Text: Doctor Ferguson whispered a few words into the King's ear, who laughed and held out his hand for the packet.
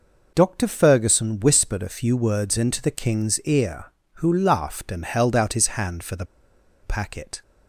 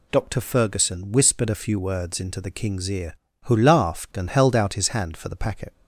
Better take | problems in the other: second | pauses between "the" and "packet"; noticeable; at 6.2 s; 0.58 s long

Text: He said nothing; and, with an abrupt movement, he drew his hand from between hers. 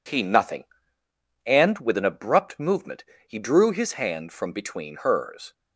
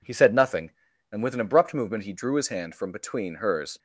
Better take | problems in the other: second | skips "said"; at 0.2 s

